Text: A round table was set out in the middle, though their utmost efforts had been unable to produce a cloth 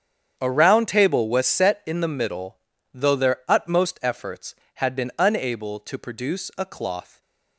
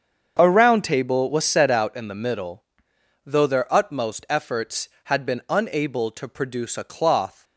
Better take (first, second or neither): second